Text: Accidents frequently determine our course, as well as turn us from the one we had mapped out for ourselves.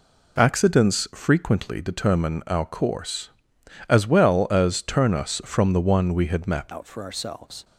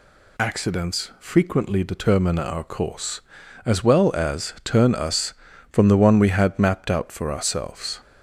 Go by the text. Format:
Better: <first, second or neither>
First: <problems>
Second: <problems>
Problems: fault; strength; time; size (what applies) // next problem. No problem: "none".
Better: second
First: changes voice at "out"; from 6.7 s on; 0.9 s long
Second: none